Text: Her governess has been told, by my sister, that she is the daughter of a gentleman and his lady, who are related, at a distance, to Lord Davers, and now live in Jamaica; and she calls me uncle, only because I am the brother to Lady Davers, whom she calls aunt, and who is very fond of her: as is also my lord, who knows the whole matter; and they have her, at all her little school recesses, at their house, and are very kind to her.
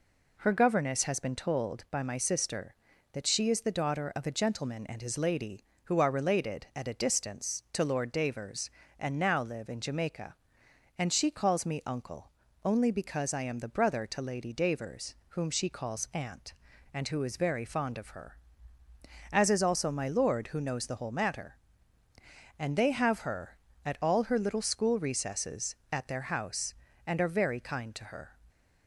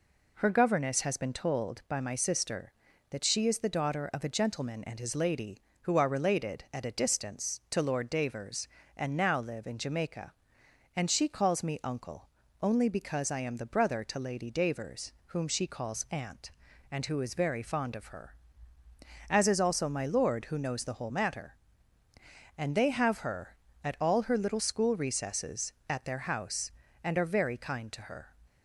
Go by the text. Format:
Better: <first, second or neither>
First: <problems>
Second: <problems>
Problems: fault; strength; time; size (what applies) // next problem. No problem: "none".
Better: neither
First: none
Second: none